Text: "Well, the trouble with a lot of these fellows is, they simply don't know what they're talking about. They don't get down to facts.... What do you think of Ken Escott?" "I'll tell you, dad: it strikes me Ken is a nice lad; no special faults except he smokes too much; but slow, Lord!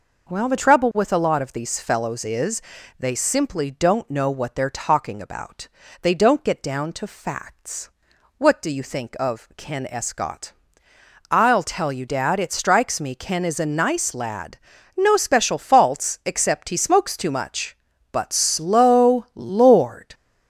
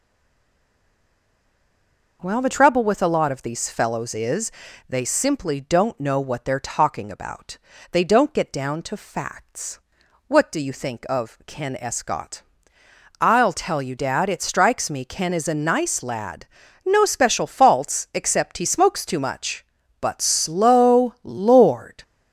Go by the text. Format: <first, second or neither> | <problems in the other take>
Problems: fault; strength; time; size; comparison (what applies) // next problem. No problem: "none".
first | stays silent before the first word; until 2.2 s; 2.2 s long